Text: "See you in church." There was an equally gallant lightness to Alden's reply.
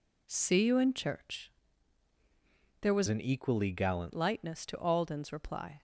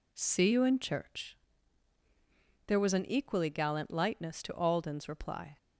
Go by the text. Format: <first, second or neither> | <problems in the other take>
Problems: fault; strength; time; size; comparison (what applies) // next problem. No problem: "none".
second | changes voice from "an" to "gallant"; from 3.0 to 4.1 s; 1.1 s long